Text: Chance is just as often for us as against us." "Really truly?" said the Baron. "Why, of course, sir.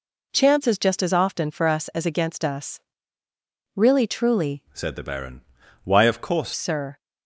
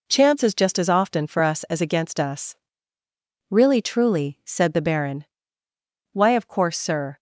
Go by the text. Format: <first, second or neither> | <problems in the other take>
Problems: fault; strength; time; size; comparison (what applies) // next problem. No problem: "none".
second | changes voice from "said" to "course"; from 4.7 to 6.5 s; 1.8 s long